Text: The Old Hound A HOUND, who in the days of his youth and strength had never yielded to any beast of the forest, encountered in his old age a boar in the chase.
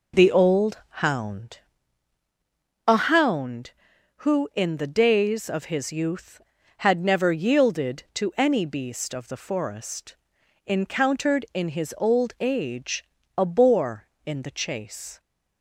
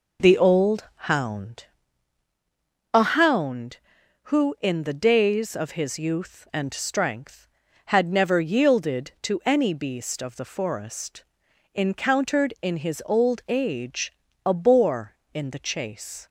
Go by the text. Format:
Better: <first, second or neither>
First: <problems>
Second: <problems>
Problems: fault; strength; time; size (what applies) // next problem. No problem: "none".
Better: second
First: pauses between "Old" and "Hound"; slight; at 0.7 s; 0.26 s long // pauses between "Hound" and "A"; strong; at 1.5 s; 1.2 s long // skips "and strength"; at 6.5 s // pauses between "age" and "a"; slight; at 13.0 s; 0.32 s long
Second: pauses between "Old" and "Hound"; slight; at 0.8 s; 0.26 s long // pauses between "Hound" and "A"; strong; at 1.6 s; 1.2 s long // pauses between "age" and "a"; slight; at 14.1 s; 0.32 s long